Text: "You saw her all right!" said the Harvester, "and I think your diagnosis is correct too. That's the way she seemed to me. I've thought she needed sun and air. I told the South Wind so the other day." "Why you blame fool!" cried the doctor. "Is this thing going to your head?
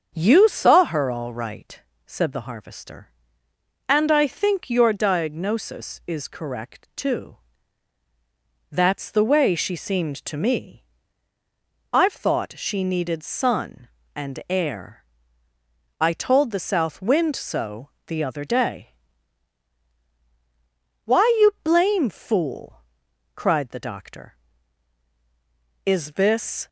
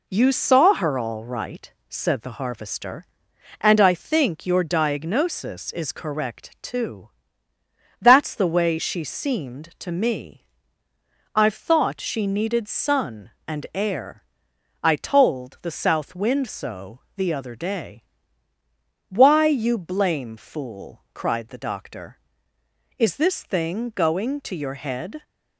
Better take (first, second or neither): second